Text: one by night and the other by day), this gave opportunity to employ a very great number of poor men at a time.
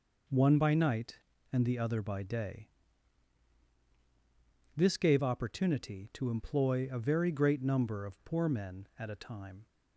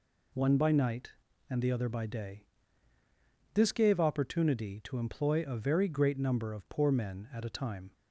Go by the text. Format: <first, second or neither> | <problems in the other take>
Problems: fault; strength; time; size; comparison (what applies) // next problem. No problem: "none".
neither | none